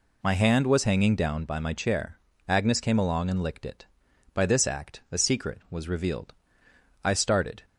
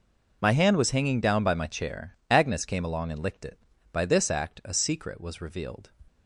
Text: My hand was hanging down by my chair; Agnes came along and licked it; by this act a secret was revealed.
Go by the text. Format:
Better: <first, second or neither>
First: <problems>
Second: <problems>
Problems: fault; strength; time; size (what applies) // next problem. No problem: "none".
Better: second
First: goes on to say "I started"; from 7.0 s on; 0.56 s long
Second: none